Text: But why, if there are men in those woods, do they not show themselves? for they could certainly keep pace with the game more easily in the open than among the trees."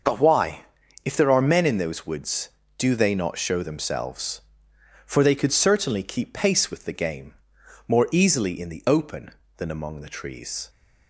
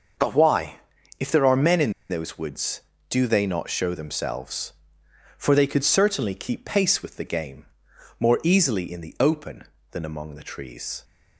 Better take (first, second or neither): first